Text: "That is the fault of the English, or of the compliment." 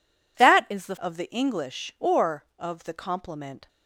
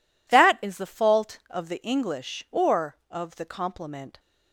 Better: second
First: skips "fault"; at 0.9 s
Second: none

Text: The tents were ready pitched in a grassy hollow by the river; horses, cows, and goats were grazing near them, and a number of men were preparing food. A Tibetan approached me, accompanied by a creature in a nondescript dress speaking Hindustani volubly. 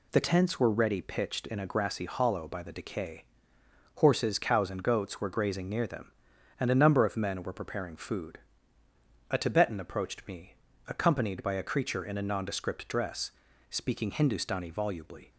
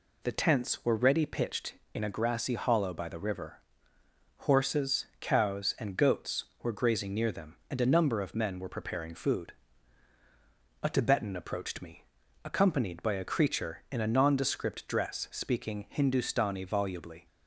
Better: second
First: says "decay" for "river"; at 2.7 s // pauses between "dress" and "speaking"; at 13.2 s; 0.40 s long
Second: none

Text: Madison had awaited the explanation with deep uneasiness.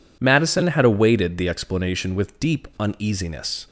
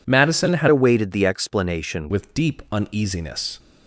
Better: first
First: none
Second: changes voice from "awaited" to "explanation"; from 0.6 to 2.0 s; 1.4 s long

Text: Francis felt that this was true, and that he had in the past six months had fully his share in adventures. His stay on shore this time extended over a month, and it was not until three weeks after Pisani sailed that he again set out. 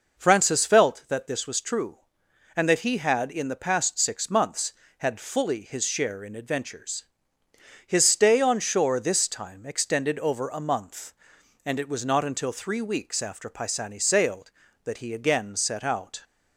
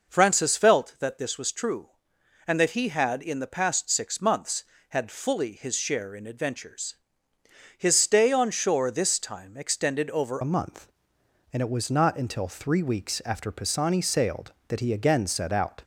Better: first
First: none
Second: changes voice at "a"; from 10.4 s on; 5.4 s long

